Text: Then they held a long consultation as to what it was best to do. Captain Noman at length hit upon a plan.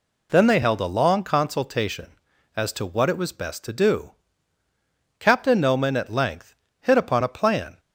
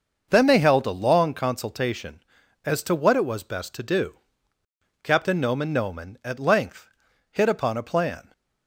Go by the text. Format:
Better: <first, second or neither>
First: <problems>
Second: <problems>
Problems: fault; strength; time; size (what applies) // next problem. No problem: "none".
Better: first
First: pauses between "length" and "hit"; slight; at 6.5 s; 0.26 s long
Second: starts louder than the rest; noticeable; until 1.3 s; 6 dB // says "Noman" twice; at 5.7 s // pauses between "length" and "hit"; at 6.8 s; 0.42 s long